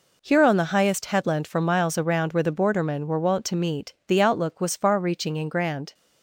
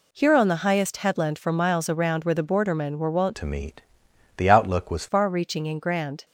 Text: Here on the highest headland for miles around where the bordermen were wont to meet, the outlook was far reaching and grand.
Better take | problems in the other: first | changes voice from "to" to "was"; from 3.3 to 5.0 s; 1.7 s long

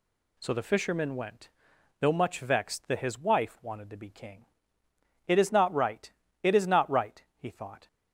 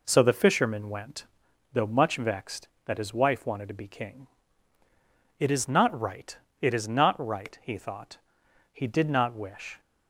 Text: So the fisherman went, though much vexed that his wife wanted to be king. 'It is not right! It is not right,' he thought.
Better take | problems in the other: first | goes on to say "He did not wish"; noticeable; from 8.7 s on; 1.0 s long

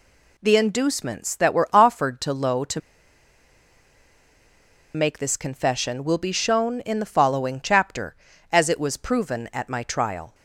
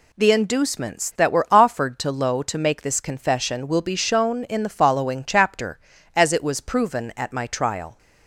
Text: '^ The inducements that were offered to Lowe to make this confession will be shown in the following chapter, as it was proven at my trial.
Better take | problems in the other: second | pauses between "to" and "make"; strong; at 2.7 s; 2.1 s long

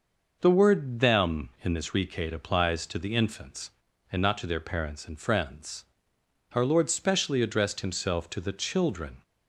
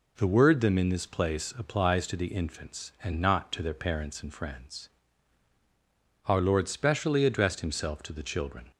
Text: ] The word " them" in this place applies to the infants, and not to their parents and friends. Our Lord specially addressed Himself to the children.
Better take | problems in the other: second | says "recate" for "place"; at 1.9 s

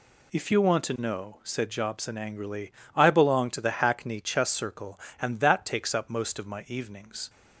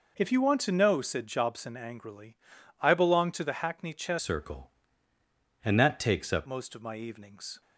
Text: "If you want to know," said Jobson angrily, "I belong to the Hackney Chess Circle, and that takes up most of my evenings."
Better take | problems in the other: first | changes voice from "Circle" to "up"; from 4.1 to 6.4 s; 2.3 s long

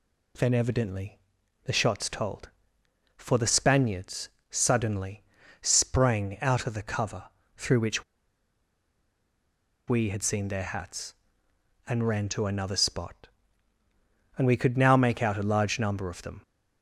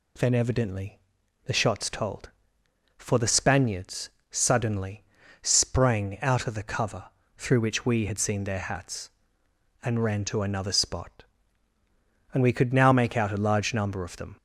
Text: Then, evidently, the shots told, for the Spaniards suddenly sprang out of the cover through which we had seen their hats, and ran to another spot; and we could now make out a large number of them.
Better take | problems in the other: second | pauses between "Spaniards" and "suddenly"; slight; at 4.2 s; 0.22 s long; slight in the second // pauses between "suddenly" and "sprang"; at 5.2 s; 0.40 s long; also in the second // pauses between "cover" and "through"; slight; at 7.2 s; 0.32 s long; slight in the second // pauses between "which" and "we"; strong; at 8.0 s; 1.8 s long

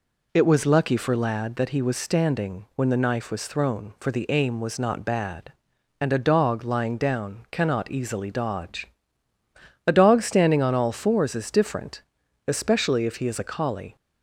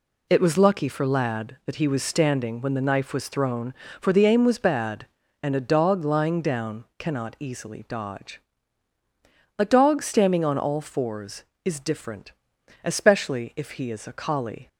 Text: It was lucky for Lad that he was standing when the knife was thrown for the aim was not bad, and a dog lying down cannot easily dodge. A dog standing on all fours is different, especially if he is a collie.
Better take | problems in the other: first | skips "not"; at 4.5 s

